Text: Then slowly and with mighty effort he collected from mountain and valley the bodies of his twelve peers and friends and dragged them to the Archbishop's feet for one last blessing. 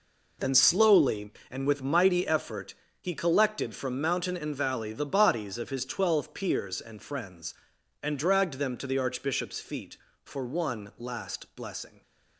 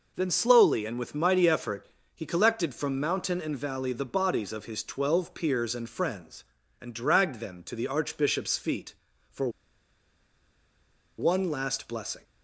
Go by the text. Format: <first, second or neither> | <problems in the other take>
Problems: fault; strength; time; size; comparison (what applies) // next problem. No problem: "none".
first | pauses between "effort" and "he"; slight; at 1.8 s; 0.26 s long; slight in the first // pauses between "for" and "one"; strong; at 9.4 s; 1.6 s long